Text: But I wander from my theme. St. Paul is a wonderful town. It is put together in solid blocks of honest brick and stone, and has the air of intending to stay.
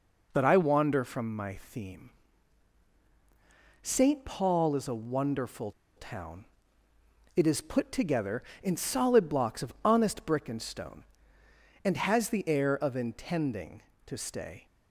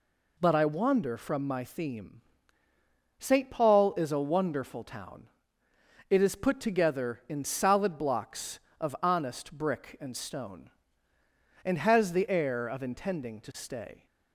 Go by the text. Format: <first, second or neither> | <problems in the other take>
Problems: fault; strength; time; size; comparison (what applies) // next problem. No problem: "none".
second | pauses between "wonderful" and "town"; slight; at 5.7 s; 0.26 s long